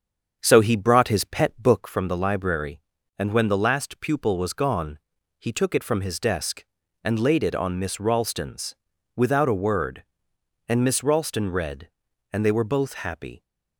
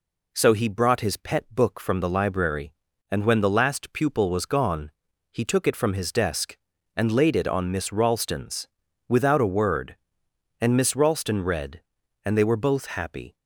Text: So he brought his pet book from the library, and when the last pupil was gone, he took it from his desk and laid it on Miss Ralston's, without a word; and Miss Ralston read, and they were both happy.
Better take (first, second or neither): second